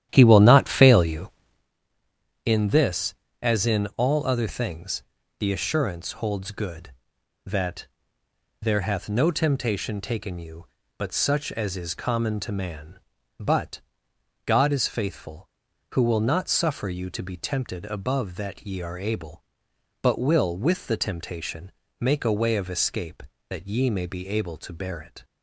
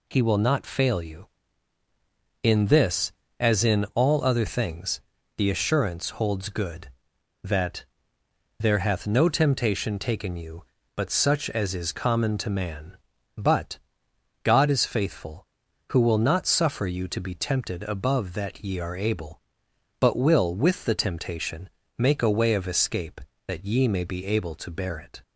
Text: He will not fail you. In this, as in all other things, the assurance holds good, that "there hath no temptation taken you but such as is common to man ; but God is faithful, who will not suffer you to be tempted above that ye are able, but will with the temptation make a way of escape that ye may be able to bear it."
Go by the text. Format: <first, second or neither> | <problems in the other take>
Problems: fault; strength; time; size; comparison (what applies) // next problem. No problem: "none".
second | starts louder than the rest; strong; until 1.7 s; 11.5 dB // pauses between "that" and "there"; noticeable; at 7.8 s; 0.74 s long; noticeable in the second // pauses between "but" and "God"; noticeable; at 13.8 s; 0.66 s long; noticeable in the second // pauses between "temptation" and "make"; slight; at 21.7 s; 0.28 s long; slight in the second